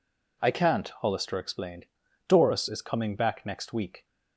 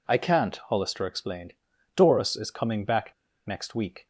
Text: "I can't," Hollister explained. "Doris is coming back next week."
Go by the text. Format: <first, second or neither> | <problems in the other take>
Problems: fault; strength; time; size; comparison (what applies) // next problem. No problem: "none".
first | pauses between "back" and "next"; slight; at 3.1 s; 0.33 s long